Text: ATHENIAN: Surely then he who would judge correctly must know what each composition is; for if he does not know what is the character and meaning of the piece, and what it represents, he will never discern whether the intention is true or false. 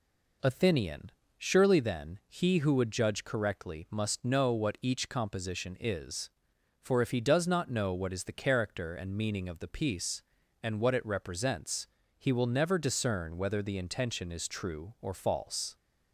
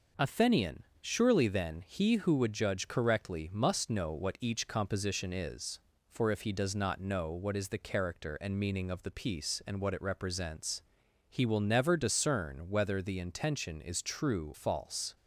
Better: first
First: none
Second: skips "or"; at 14.5 s

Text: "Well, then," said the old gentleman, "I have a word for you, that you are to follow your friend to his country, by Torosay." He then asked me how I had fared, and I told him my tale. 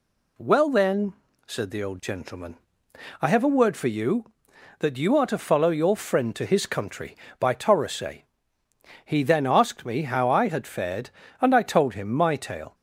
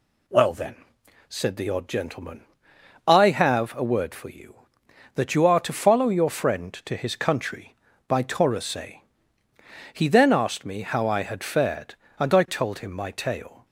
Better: first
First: none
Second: says "odd" for "old"; at 1.6 s

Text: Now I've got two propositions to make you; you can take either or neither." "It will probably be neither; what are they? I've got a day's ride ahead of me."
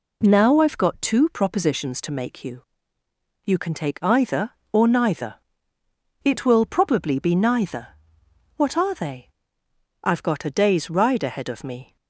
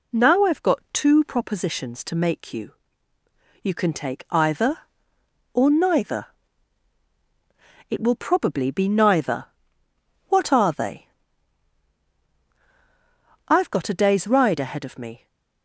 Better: neither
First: none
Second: none

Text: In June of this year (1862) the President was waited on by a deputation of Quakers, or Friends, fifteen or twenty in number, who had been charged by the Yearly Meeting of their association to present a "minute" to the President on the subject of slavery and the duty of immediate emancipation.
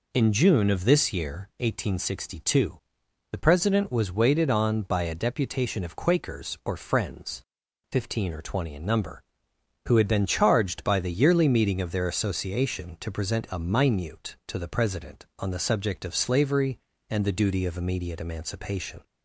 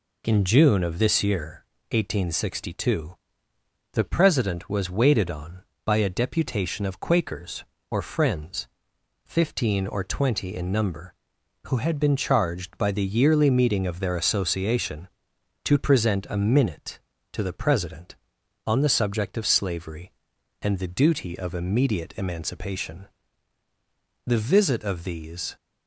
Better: first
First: none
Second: goes on to say "The visit of these"; noticeable; from 24.2 s on; 1.3 s long

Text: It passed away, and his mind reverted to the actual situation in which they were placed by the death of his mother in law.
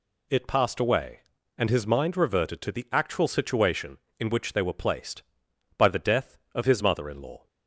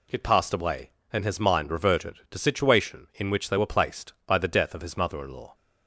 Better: first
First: none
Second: skips "the actual"; at 2.3 s

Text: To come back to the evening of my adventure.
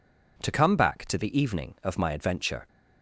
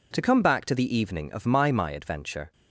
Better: first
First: none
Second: says "my" twice; at 1.7 s

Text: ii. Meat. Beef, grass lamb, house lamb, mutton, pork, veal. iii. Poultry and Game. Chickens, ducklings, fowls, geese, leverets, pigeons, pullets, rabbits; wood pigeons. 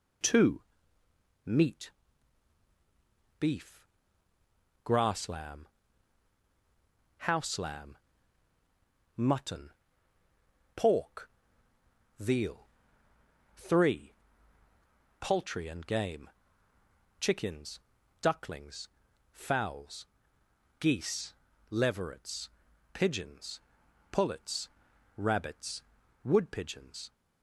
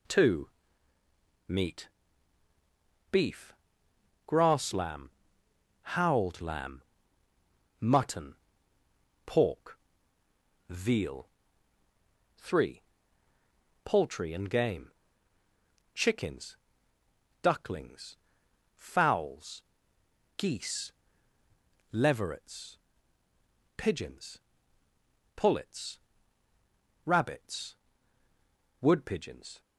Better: first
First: none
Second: says "howled" for "house"; at 5.8 s

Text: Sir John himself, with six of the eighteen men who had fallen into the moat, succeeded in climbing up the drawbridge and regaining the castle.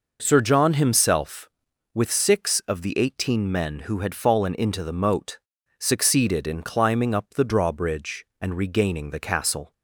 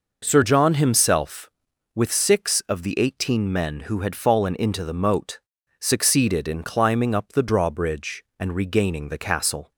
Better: neither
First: none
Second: none

